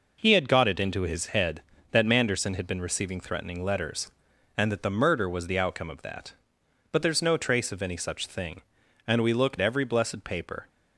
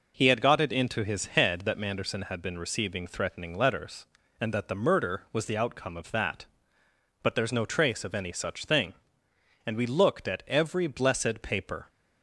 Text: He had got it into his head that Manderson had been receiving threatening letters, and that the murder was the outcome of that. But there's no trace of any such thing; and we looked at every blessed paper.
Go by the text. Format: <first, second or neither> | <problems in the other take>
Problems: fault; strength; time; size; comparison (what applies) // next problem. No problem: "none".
second | skips "at"; at 9.5 s